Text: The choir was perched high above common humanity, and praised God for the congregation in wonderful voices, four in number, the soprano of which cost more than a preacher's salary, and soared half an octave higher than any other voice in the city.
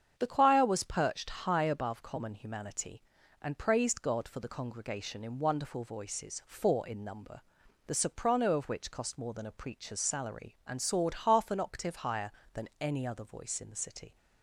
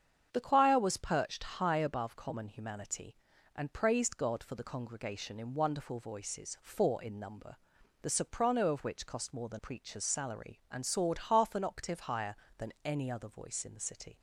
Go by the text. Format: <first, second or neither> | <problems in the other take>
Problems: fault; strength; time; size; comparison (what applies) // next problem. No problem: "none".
first | starts louder than the rest; strong; until 1.3 s; 7.5 dB; strong in the first // skips "a"; at 9.5 s